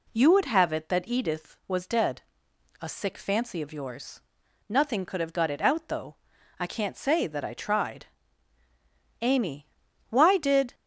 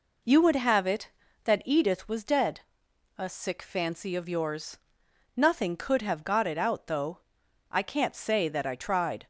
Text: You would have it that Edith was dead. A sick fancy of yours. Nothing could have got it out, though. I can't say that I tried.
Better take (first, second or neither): second